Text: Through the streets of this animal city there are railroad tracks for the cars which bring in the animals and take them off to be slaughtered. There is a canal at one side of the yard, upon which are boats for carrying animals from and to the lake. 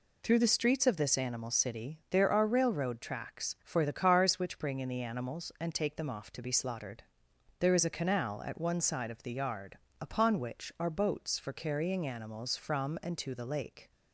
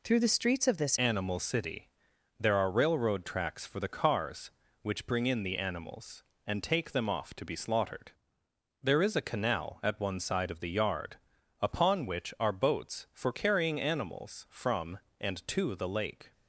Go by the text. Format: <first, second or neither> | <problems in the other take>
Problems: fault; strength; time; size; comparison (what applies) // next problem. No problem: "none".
first | changes voice at "animal"; from 0.9 s on; 15.4 s long // pauses between "city" and "there"; noticeable; at 1.8 s; 0.50 s long